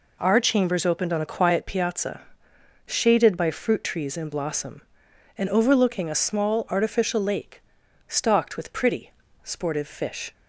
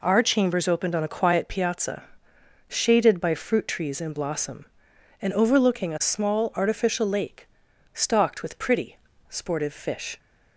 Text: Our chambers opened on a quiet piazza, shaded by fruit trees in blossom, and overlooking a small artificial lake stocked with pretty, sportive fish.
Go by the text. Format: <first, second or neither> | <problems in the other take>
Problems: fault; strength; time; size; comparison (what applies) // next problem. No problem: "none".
neither | pauses between "lake" and "stocked"; the same in both